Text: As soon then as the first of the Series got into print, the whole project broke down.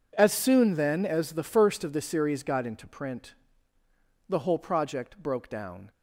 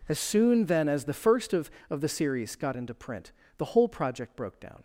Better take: first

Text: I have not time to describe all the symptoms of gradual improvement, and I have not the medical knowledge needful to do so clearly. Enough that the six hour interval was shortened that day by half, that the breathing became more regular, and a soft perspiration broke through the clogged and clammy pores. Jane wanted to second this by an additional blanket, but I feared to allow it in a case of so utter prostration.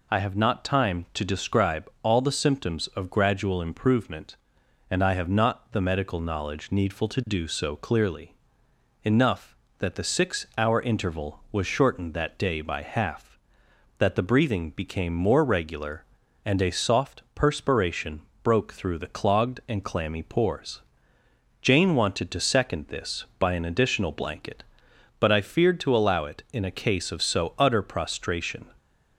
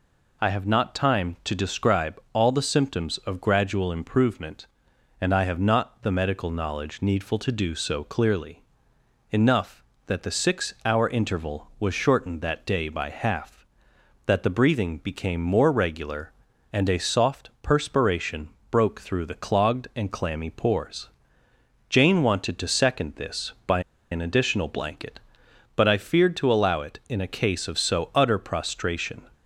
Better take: first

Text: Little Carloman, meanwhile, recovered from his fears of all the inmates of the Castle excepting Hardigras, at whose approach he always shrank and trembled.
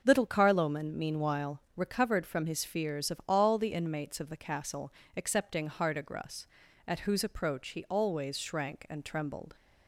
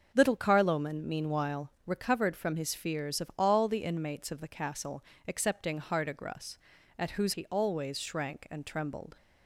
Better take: first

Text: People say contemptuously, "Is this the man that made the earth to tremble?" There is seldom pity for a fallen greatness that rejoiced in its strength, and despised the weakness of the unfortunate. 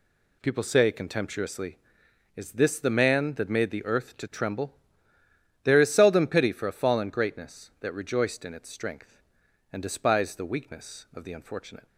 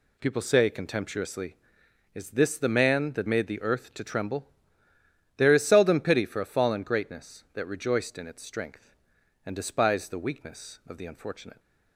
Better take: neither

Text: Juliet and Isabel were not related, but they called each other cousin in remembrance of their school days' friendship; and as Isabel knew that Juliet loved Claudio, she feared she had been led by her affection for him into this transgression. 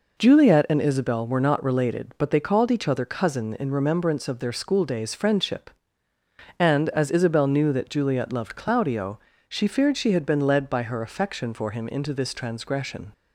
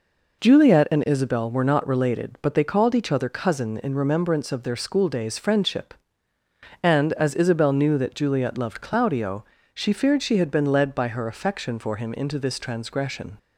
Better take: neither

